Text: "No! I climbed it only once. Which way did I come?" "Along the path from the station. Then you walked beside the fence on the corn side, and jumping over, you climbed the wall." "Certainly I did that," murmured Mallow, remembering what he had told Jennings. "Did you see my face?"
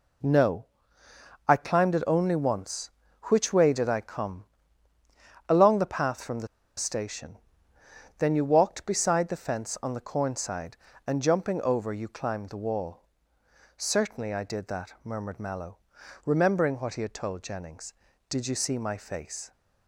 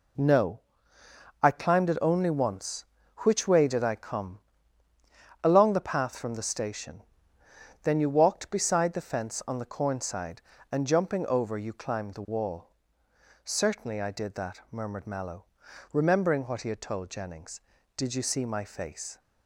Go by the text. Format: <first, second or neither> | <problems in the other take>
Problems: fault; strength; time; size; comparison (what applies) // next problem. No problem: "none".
second | pauses between "the" and "station"; slight; at 6.4 s; 0.30 s long